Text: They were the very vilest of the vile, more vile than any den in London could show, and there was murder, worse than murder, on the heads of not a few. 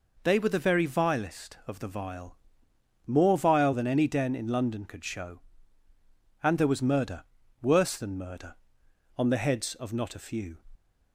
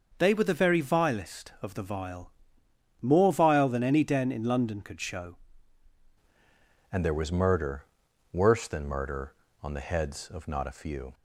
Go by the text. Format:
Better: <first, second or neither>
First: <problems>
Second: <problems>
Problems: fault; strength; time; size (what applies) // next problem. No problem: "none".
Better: first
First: none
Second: starts louder than the rest; noticeable; until 1.1 s; 6 dB // changes voice at "and"; from 6.9 s on; 4.2 s long